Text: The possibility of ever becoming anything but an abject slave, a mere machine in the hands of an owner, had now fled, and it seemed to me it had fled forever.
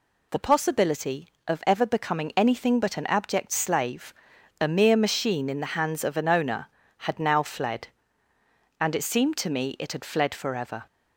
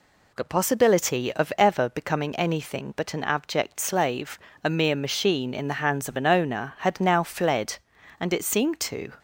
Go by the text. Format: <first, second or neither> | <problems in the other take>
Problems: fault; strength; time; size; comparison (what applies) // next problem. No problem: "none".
first | stops before "me it had fled forever"; at 9.1 s